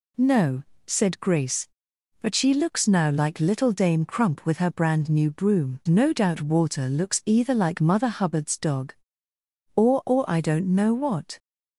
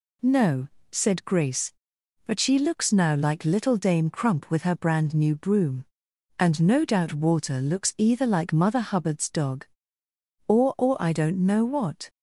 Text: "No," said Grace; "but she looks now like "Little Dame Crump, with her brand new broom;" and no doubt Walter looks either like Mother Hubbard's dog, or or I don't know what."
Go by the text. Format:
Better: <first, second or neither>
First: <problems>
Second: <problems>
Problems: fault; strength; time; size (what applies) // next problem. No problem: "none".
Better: second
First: skips "and"; at 5.8 s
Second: none